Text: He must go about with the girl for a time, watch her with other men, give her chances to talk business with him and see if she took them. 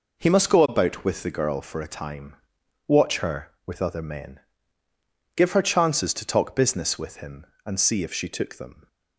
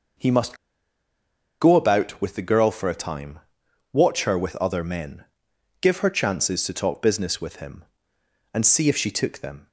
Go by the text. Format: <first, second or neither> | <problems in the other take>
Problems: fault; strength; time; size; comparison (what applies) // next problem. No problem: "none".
first | pauses between "must" and "go"; at 0.5 s; 1.0 s long